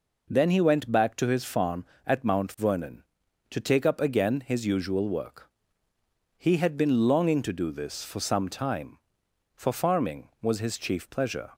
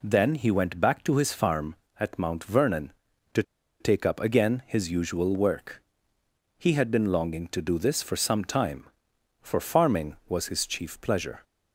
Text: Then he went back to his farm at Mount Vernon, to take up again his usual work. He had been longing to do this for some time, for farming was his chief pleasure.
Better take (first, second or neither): first